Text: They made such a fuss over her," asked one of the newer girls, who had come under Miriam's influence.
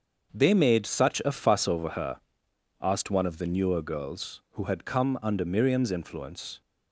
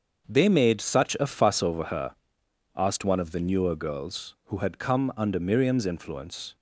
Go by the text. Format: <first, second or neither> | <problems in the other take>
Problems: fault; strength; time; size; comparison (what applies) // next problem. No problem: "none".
neither | starts louder than the rest; the same in both